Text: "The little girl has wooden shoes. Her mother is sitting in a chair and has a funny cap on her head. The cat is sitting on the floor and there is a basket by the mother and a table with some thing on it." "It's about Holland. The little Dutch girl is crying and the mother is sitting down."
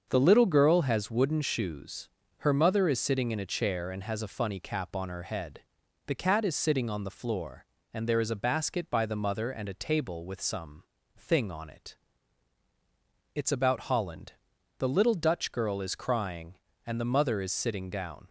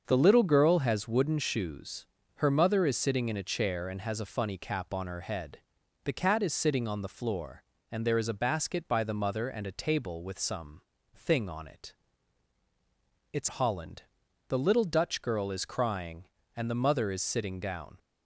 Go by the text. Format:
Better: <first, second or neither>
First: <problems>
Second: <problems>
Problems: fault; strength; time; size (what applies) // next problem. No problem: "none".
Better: first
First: starts louder than the rest; until 1.0 s; 6.5 dB // pauses between "some" and "thing"; slight; at 10.8 s; 0.30 s long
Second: starts louder than the rest; until 1.0 s; 6.5 dB // pauses between "some" and "thing"; slight; at 10.8 s; 0.30 s long // skips "about"; at 13.4 s